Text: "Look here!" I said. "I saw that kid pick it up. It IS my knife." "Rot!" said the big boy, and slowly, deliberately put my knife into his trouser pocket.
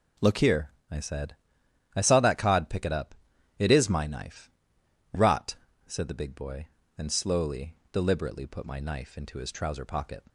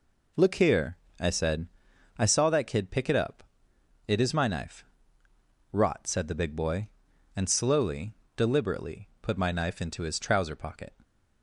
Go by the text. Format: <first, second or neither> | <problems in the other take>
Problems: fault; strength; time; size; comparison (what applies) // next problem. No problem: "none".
second | says "cod" for "kid"; at 2.3 s